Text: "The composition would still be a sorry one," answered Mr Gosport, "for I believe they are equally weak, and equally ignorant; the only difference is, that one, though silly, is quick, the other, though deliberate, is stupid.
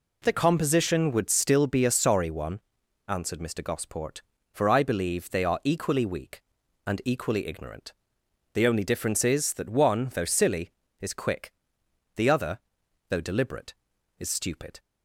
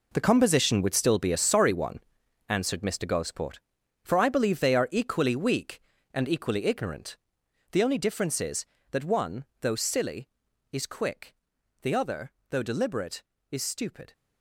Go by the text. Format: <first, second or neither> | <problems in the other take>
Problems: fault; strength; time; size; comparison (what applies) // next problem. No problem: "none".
first | gets quieter; strong; throughout; 12.5 dB